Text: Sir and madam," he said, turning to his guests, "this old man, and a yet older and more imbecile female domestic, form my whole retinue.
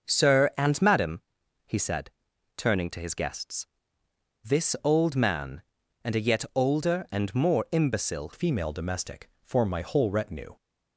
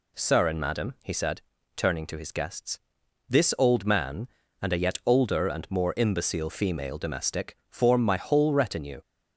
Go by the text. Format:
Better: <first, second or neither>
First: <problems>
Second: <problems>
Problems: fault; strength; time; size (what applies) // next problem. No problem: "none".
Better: second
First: starts louder than the rest; until 1.1 s; 6.5 dB // changes voice at "female"; from 8.3 s on; 2.2 s long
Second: none